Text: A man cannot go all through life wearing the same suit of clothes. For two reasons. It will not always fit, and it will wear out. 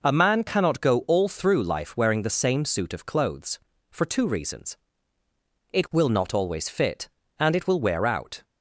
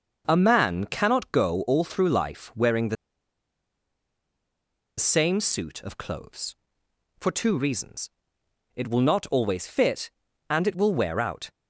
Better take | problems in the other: first | starts louder than the rest; until 1.2 s; 6 dB // pauses between "the" and "same"; strong; at 2.9 s; 2.0 s long

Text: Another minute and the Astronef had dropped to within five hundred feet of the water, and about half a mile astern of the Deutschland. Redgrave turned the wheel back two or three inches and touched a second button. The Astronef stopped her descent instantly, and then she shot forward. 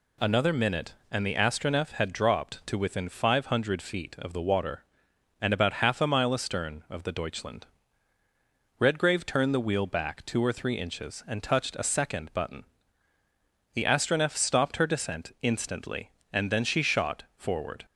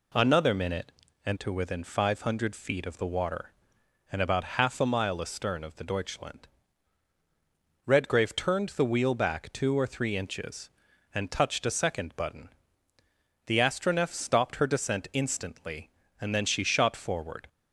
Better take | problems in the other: first | skips "the Astronef had dropped"; at 1.3 s

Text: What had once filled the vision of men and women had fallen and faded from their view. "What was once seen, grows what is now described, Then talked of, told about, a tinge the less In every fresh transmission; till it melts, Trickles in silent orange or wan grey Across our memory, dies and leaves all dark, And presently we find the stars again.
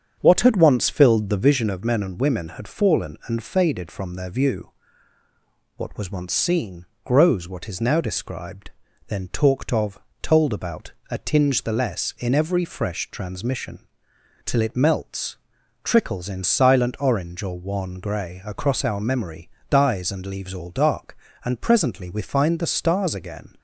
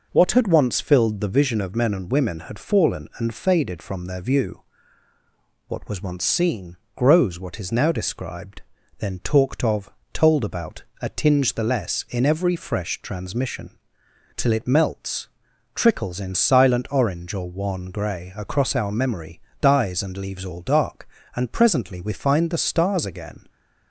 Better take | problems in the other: second | starts louder than the rest; strong; until 1.8 s; 7.5 dB

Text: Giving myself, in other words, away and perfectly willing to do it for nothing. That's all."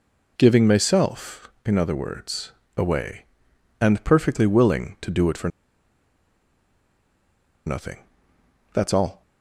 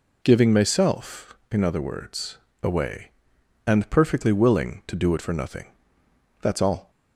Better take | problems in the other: second | pauses between "for" and "nothing"; strong; at 5.4 s; 2.1 s long

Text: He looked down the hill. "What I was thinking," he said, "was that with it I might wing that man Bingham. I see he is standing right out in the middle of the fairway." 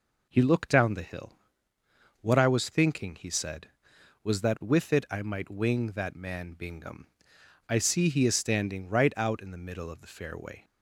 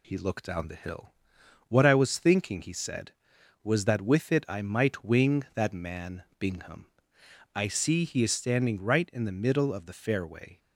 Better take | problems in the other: first | pauses between "man" and "Bingham"; slight; at 6.2 s; 0.16 s long // skips "out"; at 9.1 s

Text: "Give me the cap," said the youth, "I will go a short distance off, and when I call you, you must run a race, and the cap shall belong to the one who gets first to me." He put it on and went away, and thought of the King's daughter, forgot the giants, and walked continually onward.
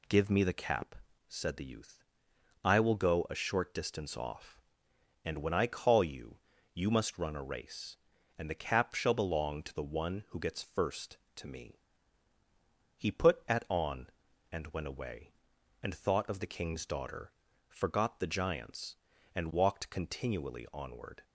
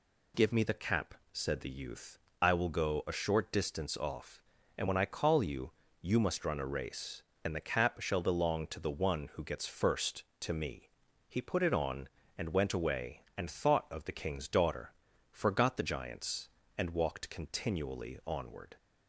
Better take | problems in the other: second | says "at" for "it"; at 13.4 s

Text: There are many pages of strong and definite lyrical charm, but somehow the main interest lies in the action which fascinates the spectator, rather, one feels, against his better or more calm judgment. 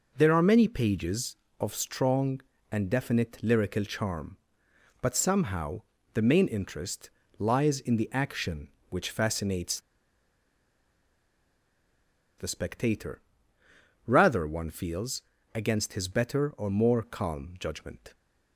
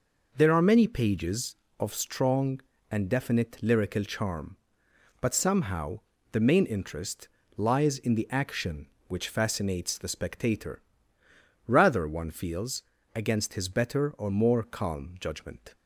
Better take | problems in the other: second | pauses between "somehow" and "the"; slight; at 5.8 s; 0.32 s long; slight in the second // pauses between "interest" and "lies"; slight; at 7.0 s; 0.30 s long; slight in the second // pauses between "fascinates" and "the"; strong; at 9.7 s; 2.5 s long

